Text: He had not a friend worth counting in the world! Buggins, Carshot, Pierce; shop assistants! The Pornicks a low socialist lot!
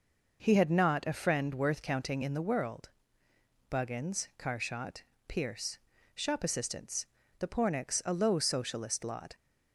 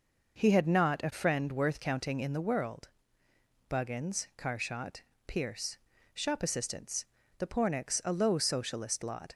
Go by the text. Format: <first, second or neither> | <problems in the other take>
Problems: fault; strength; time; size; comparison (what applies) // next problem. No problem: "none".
neither | none